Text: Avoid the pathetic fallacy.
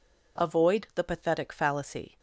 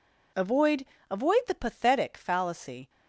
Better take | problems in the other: first | says "Avoid" twice; at 1.1 s

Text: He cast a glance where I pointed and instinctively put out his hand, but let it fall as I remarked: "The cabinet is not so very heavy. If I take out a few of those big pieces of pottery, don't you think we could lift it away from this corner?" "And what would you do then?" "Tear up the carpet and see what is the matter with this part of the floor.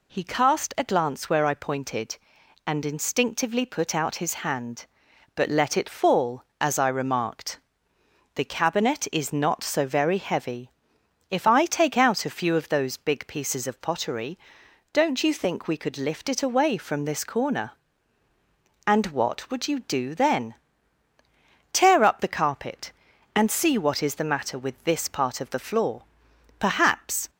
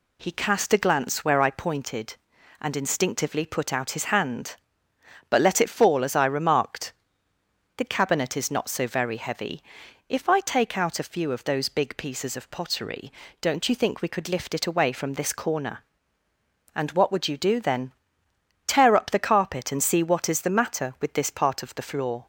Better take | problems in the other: second | goes on to say "Perhaps"; noticeable; from 26.5 s on; 0.72 s long

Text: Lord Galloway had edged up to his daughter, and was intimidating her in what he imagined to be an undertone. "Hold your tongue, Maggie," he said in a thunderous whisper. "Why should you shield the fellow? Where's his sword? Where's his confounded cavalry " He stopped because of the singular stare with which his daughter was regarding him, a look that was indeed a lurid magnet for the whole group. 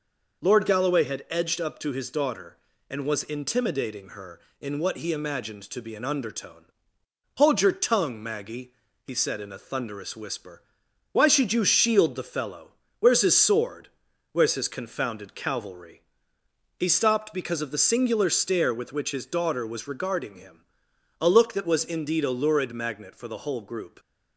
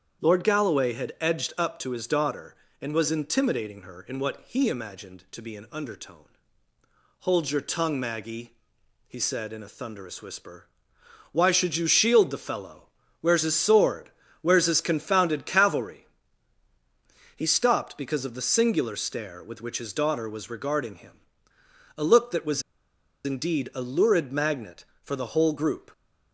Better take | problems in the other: first | starts louder than the rest; strong; until 1.3 s; 8.5 dB // pauses between "was" and "indeed"; noticeable; at 22.6 s; 0.63 s long

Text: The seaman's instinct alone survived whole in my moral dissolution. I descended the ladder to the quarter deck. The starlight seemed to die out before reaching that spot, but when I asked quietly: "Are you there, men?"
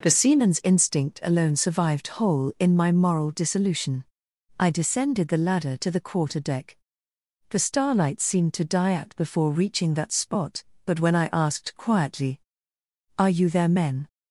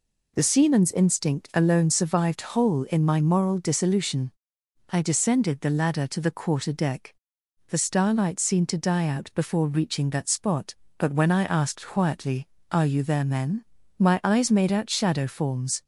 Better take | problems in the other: first | goes on to say "my eyes made out shadow forms"; strong; from 13.9 s on; 1.8 s long

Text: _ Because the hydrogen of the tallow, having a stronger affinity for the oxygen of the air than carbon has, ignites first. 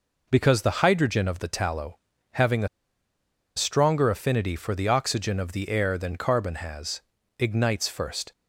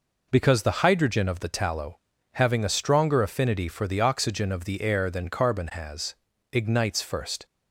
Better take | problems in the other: second | pauses between "a" and "stronger"; noticeable; at 2.6 s; 0.88 s long

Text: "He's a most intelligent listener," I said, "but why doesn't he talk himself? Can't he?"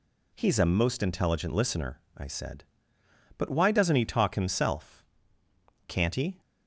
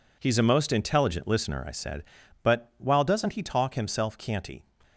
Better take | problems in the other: first | says "while" for "why"; at 2.7 s

